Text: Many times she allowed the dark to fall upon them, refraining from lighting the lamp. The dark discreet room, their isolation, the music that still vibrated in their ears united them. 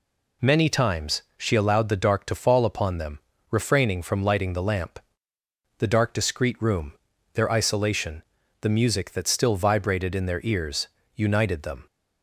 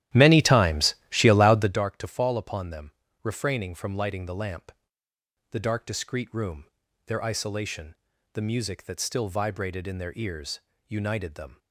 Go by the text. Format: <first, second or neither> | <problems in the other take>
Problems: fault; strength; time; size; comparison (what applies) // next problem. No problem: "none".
first | starts louder than the rest; strong; until 1.8 s; 13 dB // pauses between "times" and "she"; slight; at 0.9 s; 0.16 s long; slight in the first // pauses between "ears" and "united"; slight; at 10.6 s; 0.26 s long; slight in the first